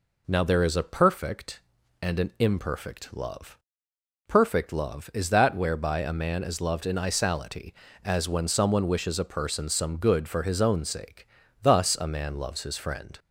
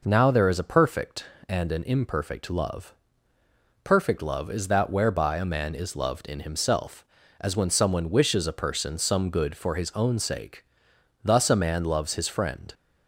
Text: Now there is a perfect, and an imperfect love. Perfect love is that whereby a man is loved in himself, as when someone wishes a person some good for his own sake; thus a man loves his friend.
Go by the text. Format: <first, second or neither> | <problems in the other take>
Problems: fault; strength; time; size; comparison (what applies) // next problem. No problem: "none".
second | says "isality" for "himself"; at 6.9 s